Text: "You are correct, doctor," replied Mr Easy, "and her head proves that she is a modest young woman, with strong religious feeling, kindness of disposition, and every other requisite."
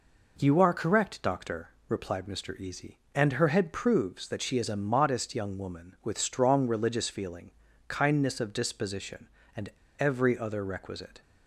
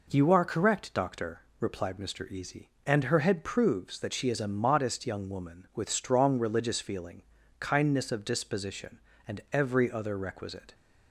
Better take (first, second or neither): second